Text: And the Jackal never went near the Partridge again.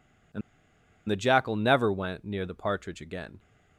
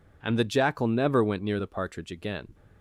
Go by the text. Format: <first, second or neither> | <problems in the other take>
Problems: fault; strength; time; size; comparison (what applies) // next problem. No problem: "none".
second | pauses between "And" and "the"; noticeable; at 0.4 s; 0.68 s long